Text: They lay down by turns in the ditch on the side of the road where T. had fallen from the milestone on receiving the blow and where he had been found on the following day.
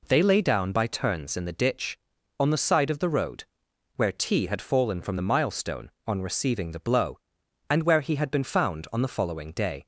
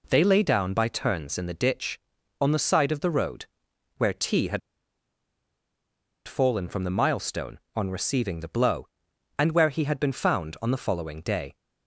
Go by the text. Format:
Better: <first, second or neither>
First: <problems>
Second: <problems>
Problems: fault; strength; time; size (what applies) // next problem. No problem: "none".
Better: first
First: pauses between "road" and "where"; noticeable; at 3.4 s; 0.52 s long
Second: pauses between "road" and "where"; noticeable; at 3.4 s; 0.52 s long // pauses between "had" and "fallen"; strong; at 4.6 s; 1.6 s long